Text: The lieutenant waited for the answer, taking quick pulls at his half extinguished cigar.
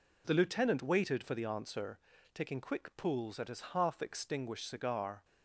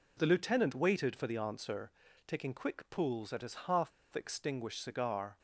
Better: first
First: none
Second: pauses between "half" and "extinguished"; slight; at 3.9 s; 0.23 s long

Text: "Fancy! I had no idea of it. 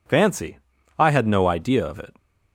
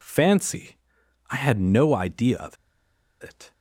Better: first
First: none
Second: pauses between "of" and "it"; noticeable; at 2.5 s; 0.66 s long

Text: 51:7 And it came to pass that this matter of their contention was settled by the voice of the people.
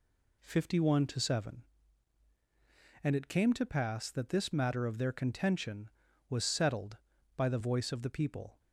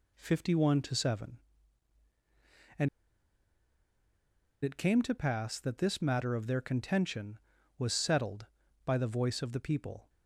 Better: first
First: none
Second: pauses between "And" and "it"; strong; at 2.8 s; 1.7 s long

